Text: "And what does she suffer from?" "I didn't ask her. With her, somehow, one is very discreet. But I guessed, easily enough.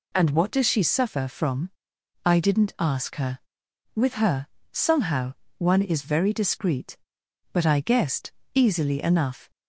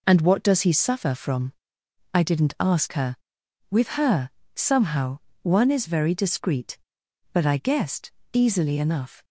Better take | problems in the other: first | says "he" for "she"; at 0.6 s

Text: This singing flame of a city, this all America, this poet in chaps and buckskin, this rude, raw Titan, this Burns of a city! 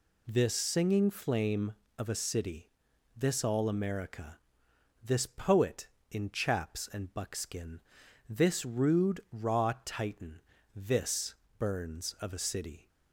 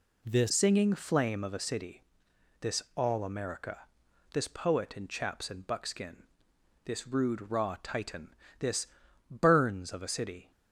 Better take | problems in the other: first | changes voice at "singing"; from 0.4 s on; 10.1 s long // pauses between "this" and "Burns"; at 8.8 s; 0.42 s long; slight in the first

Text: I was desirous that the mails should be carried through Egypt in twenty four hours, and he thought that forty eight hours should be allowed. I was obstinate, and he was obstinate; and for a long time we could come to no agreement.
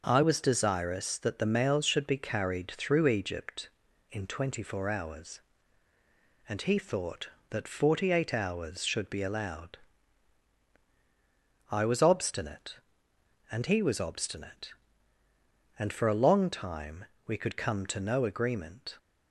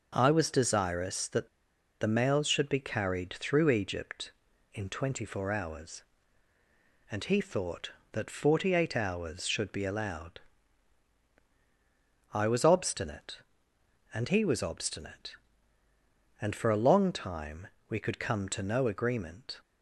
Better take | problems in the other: first | pauses between "that" and "the"; noticeable; at 1.4 s; 0.52 s long // pauses between "time" and "we"; slight; at 17.6 s; 0.20 s long; slight in the first

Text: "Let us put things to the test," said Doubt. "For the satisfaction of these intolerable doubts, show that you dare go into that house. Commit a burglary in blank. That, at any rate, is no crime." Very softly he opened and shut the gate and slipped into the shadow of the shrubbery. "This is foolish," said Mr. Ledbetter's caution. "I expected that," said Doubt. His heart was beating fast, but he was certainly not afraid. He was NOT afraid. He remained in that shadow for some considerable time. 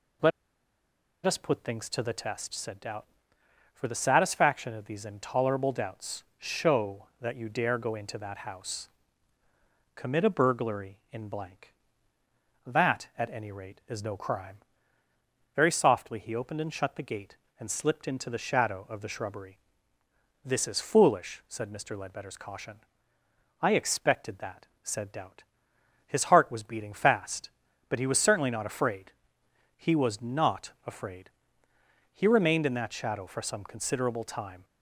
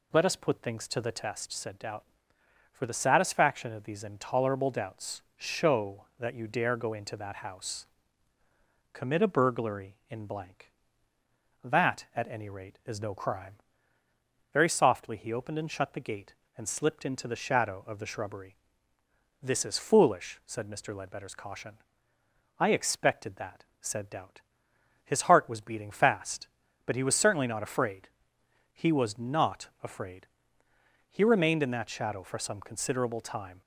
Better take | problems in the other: second | pauses between "Let" and "us"; noticeable; at 0.3 s; 0.95 s long

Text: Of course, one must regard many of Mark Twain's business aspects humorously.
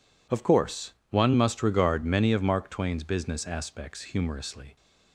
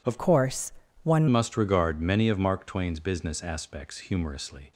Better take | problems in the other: first | changes voice from "course" to "one"; from 0.1 to 1.2 s; 1.1 s long

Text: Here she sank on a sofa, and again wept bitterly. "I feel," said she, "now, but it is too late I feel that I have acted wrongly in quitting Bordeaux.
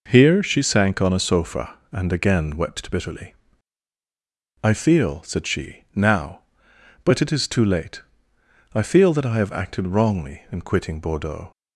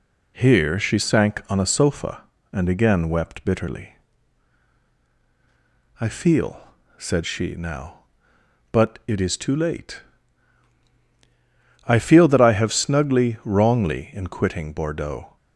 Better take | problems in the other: first | pauses between "late" and "I"; strong; at 10.0 s; 1.8 s long; noticeable in the first // says "snugly" for "acted"; at 12.7 s

